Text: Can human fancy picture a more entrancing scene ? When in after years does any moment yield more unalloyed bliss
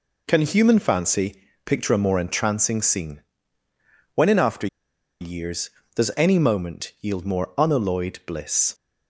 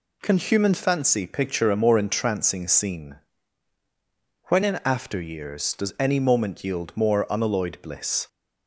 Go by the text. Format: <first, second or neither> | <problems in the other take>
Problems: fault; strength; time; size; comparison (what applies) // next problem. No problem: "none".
second | pauses between "fancy" and "picture"; slight; at 1.4 s; 0.24 s long // pauses between "after" and "years"; noticeable; at 4.6 s; 0.54 s long